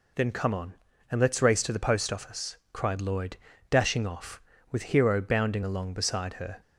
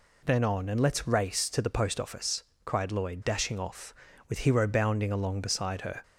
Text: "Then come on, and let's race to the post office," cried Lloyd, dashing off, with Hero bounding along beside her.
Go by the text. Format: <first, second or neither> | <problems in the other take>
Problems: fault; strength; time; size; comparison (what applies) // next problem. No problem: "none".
first | skips "come"; at 0.4 s